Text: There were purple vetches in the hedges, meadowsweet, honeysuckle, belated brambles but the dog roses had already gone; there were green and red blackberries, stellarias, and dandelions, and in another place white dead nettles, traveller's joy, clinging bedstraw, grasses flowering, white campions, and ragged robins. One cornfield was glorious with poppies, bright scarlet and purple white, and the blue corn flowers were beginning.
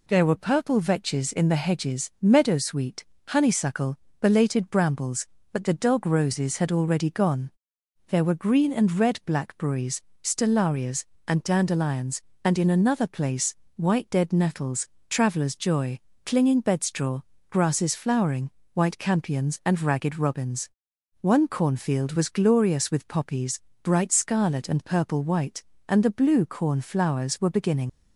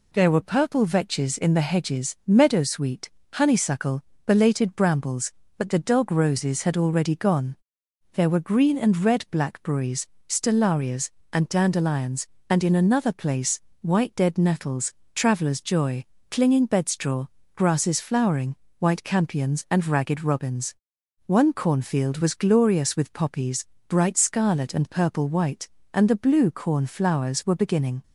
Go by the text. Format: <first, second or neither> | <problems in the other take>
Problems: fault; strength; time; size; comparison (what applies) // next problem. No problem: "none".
second | pauses between "place" and "white"; slight; at 13.5 s; 0.20 s long; slight in the second // leaves "beginning" unfinished; at 27.8 s; 75 ms